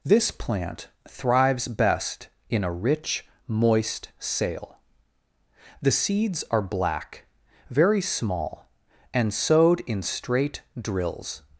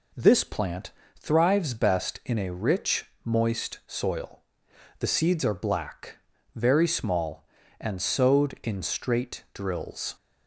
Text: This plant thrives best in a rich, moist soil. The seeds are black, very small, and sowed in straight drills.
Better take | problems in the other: second | pauses between "plant" and "thrives"; slight; at 0.8 s; 0.20 s long; slight in the second // says "sail" for "soil"; at 4.1 s // pauses between "straight" and "drills"; slight; at 10.6 s; 0.17 s long

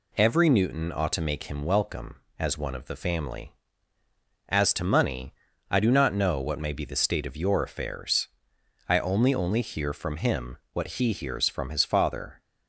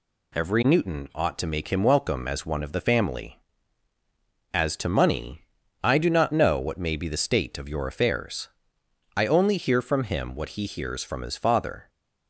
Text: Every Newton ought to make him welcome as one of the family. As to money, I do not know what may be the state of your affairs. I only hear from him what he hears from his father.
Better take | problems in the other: second | says "only" twice; at 9.3 s // pauses between "him" and "what"; slight; at 10.5 s; 0.16 s long

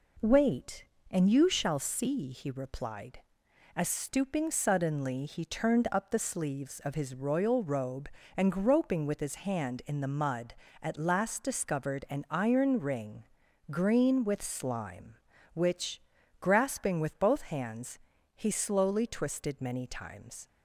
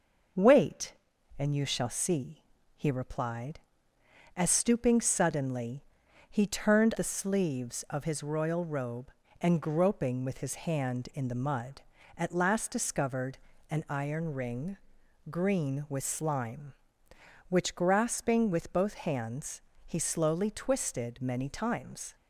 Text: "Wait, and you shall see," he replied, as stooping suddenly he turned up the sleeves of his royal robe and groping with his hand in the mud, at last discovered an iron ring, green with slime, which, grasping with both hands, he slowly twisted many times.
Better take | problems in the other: first | starts louder than the rest; until 1.8 s; 6 dB // pauses between "suddenly" and "he"; noticeable; at 5.8 s; 0.46 s long // skips "up"; at 6.9 s // pauses between "discovered" and "an"; slight; at 13.3 s; 0.32 s long

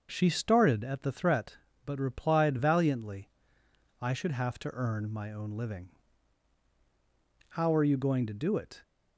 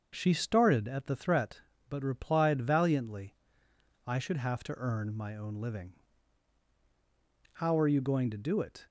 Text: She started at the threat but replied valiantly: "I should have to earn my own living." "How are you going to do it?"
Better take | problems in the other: neither | starts louder than the rest; the same in both

